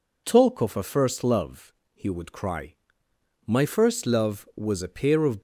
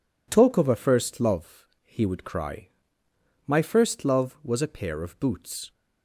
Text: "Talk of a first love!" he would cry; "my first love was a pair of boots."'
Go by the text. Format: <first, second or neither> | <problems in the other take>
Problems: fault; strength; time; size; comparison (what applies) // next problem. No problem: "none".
second | stops before "boots"; at 5.3 s